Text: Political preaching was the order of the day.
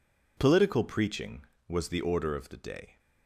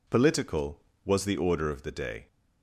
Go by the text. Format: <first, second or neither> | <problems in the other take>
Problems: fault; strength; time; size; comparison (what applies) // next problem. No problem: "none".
first | skips "preaching"; at 0.9 s